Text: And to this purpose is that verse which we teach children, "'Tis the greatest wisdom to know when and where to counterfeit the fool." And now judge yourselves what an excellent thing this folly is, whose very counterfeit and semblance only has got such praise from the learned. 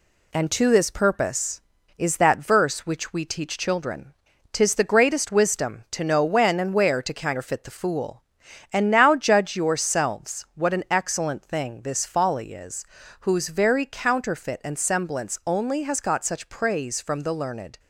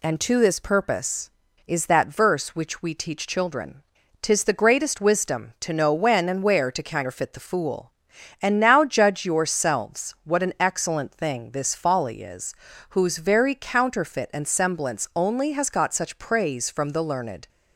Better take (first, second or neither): second